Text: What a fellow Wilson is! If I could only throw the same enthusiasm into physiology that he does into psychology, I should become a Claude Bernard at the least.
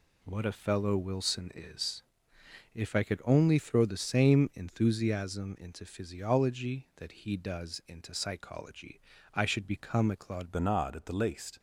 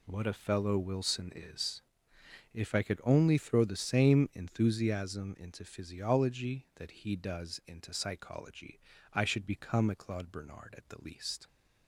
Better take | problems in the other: second | changes voice at "Bernard"; from 10.5 s on; 1.0 s long

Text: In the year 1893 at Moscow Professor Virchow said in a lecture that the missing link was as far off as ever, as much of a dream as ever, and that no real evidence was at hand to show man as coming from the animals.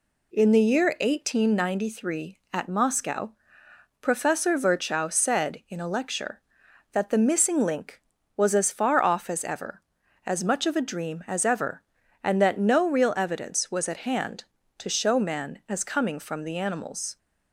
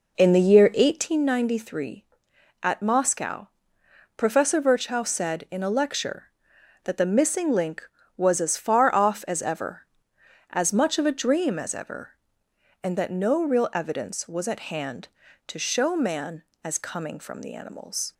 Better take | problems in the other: first | starts louder than the rest; noticeable; until 1.2 s; 4.5 dB // pauses between "Moscow" and "Professor"; noticeable; at 3.4 s; 0.68 s long; noticeable in the first

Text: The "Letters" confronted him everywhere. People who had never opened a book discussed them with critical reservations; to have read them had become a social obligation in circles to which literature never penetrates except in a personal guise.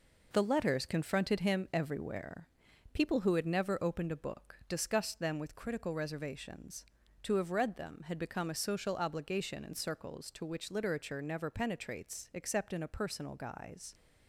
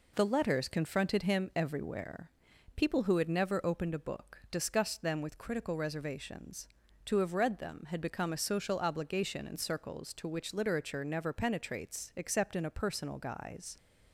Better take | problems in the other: second | gets quieter; noticeable; throughout; 6 dB

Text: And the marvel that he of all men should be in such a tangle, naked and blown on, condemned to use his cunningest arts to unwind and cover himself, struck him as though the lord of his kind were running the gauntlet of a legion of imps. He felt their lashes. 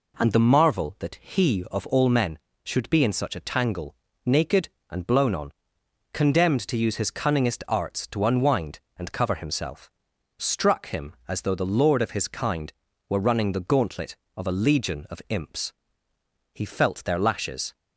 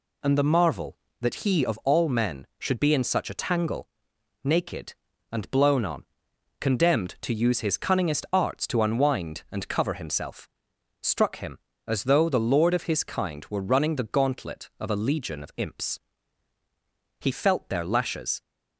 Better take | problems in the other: neither | none

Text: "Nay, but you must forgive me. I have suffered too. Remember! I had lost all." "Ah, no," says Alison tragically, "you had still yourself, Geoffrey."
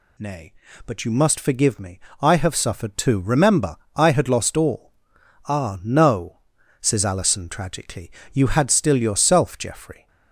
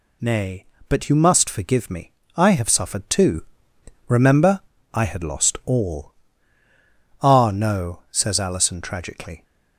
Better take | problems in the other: first | stops before "you had still yourself Geoffrey"; at 9.4 s

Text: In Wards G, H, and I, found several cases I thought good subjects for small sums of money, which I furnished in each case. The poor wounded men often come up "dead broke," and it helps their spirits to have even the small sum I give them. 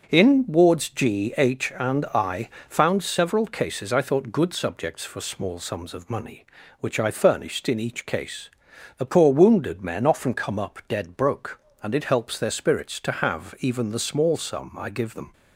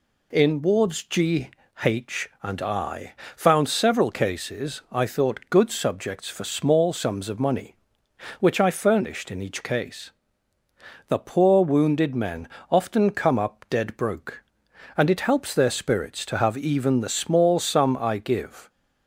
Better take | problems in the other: first | pauses between "men" and "often"; slight; at 12.4 s; 0.22 s long // stops before "them"; at 18.6 s

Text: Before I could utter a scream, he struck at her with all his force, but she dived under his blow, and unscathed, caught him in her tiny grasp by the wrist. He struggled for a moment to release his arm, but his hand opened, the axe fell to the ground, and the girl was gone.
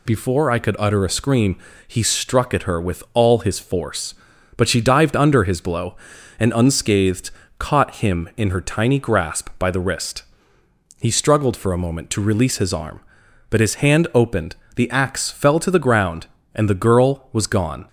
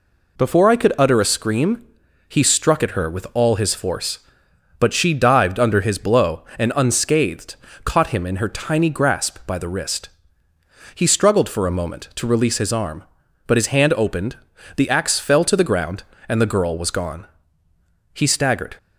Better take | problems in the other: first | goes on to say "He staggered"; noticeable; from 18.1 s on; 0.64 s long

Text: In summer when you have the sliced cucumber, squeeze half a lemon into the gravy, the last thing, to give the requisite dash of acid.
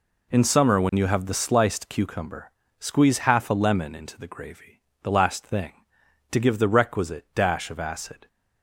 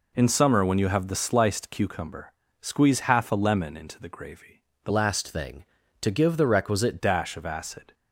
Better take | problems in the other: first | changes voice from "last" to "requisite"; from 4.8 to 6.9 s; 2.1 s long

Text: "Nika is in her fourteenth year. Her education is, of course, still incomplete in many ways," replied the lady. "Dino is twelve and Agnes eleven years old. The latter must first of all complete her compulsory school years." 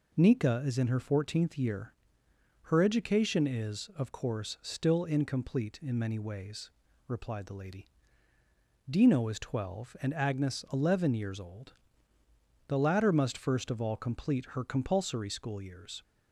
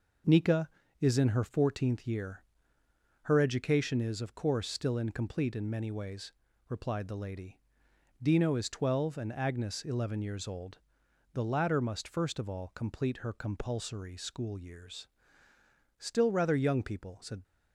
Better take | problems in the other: first | goes on to say "Still rather young people said"; from 15.9 s on; 1.4 s long

